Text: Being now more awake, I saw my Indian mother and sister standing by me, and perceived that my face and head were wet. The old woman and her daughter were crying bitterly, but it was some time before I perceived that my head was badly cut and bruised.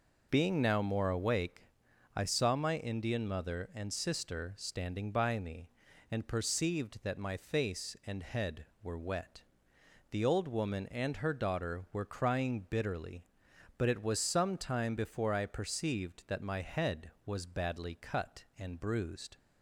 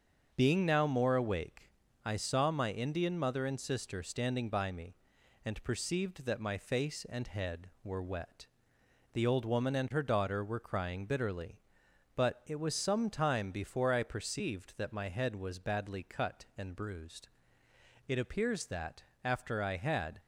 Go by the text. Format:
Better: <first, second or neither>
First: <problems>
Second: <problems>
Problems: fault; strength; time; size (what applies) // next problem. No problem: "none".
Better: first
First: none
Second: starts louder than the rest; until 1.3 s; 6.5 dB // goes on to say "It appears that after I had"; strong; from 18.0 s on; 2.1 s long